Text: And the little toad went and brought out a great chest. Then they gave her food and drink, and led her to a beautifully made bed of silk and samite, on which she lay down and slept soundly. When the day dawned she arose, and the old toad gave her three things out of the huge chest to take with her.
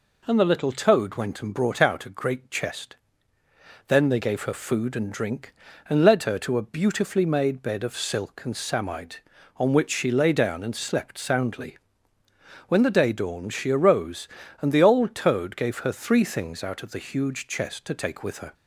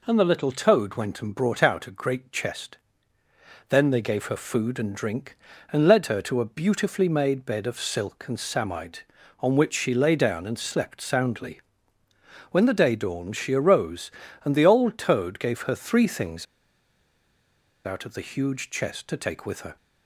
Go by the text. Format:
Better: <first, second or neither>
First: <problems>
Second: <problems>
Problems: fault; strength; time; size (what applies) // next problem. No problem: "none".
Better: first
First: none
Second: pauses between "things" and "out"; strong; at 16.4 s; 1.4 s long